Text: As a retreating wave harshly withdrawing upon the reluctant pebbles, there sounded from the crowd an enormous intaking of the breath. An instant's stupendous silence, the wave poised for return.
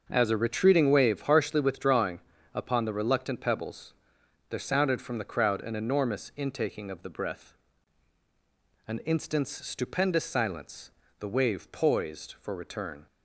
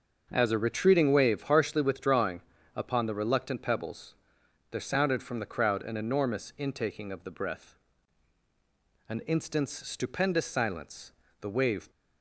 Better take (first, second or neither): first